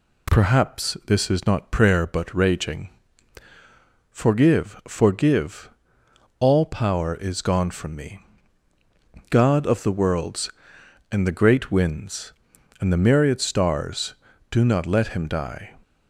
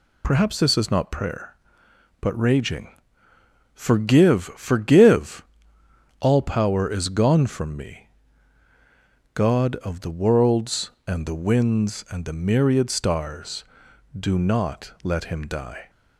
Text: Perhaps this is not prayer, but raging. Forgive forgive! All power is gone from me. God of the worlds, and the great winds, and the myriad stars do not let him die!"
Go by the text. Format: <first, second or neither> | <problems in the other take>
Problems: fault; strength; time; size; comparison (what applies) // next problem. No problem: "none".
first | skips "great"; at 11.3 s